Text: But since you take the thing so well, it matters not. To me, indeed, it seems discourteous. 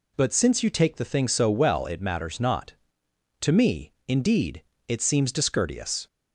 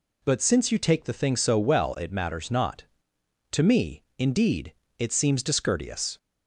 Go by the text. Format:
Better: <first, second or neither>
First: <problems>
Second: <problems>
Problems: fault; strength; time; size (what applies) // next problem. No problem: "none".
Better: neither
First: none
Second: none